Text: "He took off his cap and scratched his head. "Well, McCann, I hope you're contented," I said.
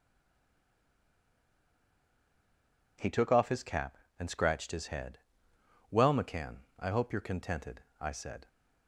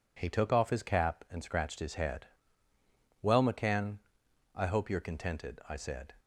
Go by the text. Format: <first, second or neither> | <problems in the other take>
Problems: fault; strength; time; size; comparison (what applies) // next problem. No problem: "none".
second | stays silent before the first word; strong; until 2.9 s; 2.9 s long